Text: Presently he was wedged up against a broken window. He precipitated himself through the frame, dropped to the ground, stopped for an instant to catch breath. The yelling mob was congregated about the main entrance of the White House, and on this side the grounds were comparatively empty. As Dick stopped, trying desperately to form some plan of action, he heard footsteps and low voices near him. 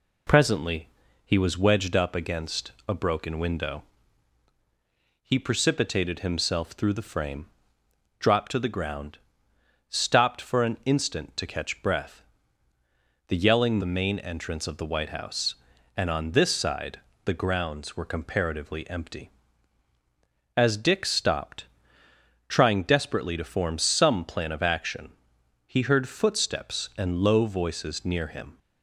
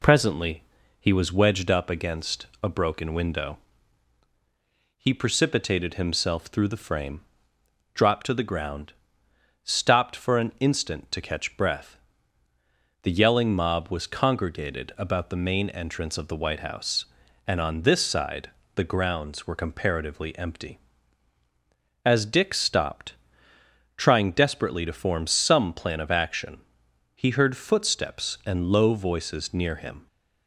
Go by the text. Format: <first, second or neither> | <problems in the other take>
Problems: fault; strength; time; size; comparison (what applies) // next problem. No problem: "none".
second | pauses between "Presently" and "he"; slight; at 0.8 s; 0.34 s long; slight in the second // pauses between "against" and "a"; slight; at 2.7 s; 0.16 s long; slight in the second // skips "mob was congregated about"; at 13.7 s // pauses between "side" and "the"; slight; at 16.9 s; 0.26 s long; slight in the second